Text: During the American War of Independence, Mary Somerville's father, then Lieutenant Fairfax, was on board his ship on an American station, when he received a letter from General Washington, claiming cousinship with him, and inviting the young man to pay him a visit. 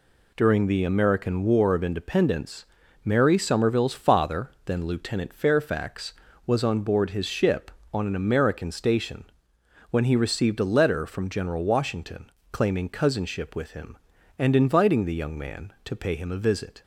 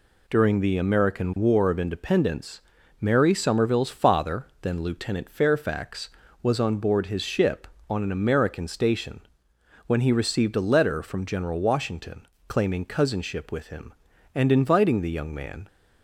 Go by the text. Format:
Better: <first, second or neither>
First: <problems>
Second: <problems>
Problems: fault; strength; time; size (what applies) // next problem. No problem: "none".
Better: first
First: none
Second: stops before "to pay him a visit"; at 15.6 s